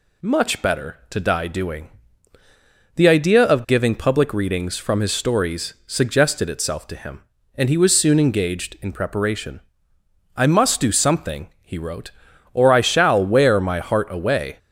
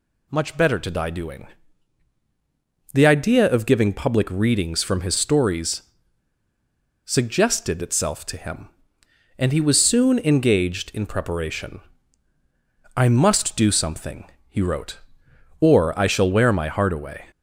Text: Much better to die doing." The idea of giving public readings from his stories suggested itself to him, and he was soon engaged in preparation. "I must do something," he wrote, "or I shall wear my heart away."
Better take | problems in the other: first | pauses between "stories" and "suggested"; at 5.8 s; 1.2 s long

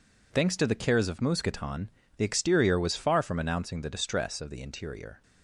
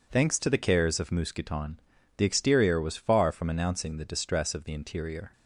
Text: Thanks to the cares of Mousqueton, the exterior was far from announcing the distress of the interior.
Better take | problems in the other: neither | none

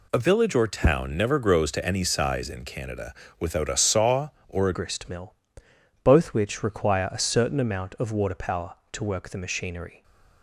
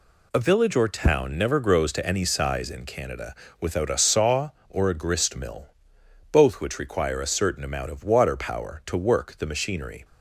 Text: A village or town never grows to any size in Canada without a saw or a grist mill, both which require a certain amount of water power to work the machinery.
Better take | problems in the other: second | pauses between "Canada" and "without"; slight; at 3.1 s; 0.26 s long; slight in the second // changes voice at "grist"; from 4.7 s on; 5.3 s long

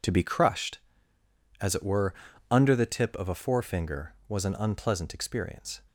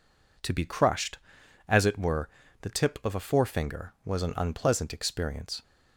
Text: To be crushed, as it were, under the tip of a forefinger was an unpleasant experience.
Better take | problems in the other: first | skips "under"; at 2.4 s

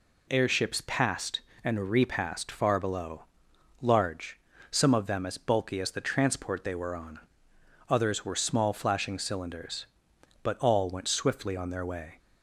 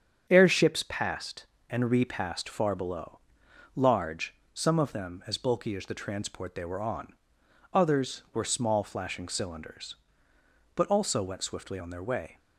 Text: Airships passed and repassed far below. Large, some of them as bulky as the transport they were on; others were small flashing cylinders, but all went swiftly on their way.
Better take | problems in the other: first | starts louder than the rest; strong; until 1.3 s; 7.5 dB // says "also" for "all"; at 10.8 s

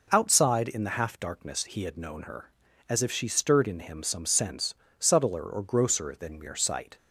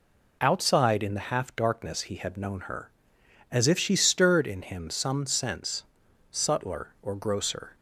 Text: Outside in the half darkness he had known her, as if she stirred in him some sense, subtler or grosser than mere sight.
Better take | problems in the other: first | stops before "than mere sight"; at 7.7 s

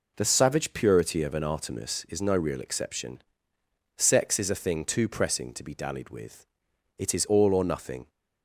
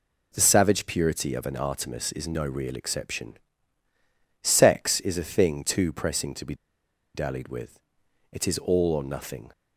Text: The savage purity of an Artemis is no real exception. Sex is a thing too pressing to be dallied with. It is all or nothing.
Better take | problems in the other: first | pauses between "be" and "dallied"; noticeable; at 6.5 s; 0.60 s long

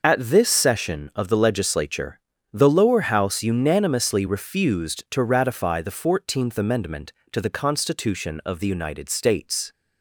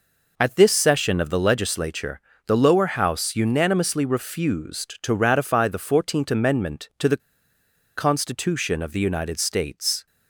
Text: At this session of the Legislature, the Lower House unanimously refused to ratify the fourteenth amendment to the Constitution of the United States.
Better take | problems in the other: first | pauses between "the" and "Constitution"; noticeable; at 7.2 s; 0.79 s long

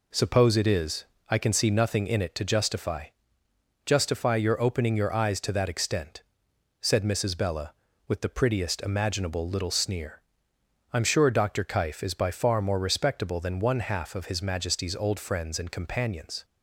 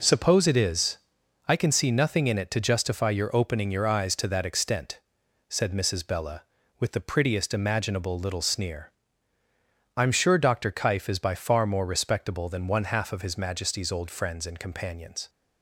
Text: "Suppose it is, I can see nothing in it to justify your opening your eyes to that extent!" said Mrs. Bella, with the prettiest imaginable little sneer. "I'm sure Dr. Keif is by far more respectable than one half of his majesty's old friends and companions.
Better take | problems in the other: second | says "justify" twice; at 3.8 s

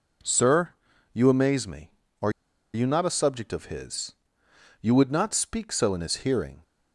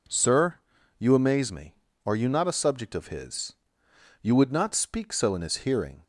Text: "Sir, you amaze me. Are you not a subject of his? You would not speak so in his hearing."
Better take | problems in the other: second | pauses between "Are" and "you"; at 2.2 s; 0.44 s long

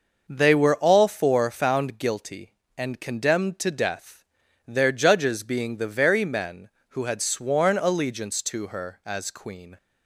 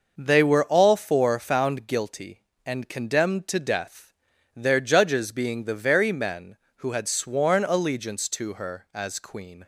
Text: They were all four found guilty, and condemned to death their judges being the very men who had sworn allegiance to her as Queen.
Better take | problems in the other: neither | pauses between "death" and "their"; the same in both

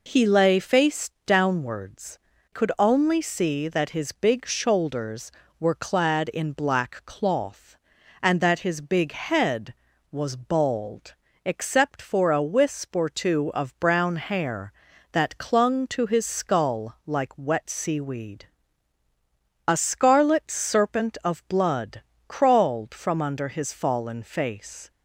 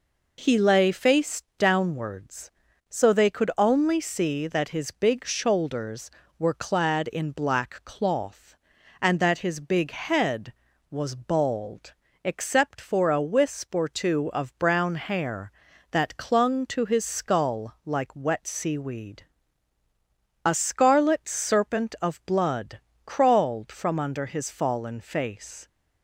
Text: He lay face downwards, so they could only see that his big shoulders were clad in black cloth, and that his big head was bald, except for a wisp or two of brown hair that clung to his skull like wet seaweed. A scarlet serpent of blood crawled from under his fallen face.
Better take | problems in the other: second | skips "so they"; at 2.3 s // pauses between "blood" and "crawled"; slight; at 21.9 s; 0.28 s long; slight in the second

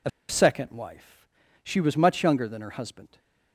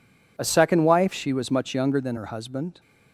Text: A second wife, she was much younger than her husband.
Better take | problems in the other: second | pauses between "A" and "second"; slight; at 0.0 s; 0.19 s long

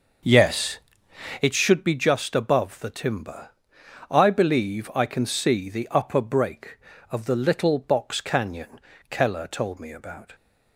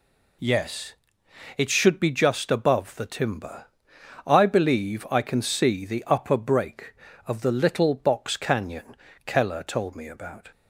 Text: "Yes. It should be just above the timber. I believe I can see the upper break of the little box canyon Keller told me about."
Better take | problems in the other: second | starts louder than the rest; until 1.5 s; 6 dB // pauses between "canyon" and "Keller"; slight; at 8.7 s; 0.30 s long; slight in the second

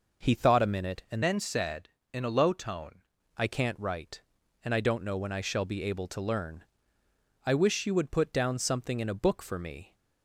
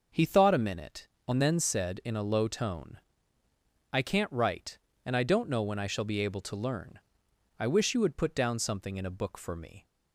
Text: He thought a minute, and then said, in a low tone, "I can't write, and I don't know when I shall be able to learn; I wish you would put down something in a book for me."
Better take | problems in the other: second | changes voice from "then" to "tone"; from 1.2 to 3.0 s; 1.8 s long

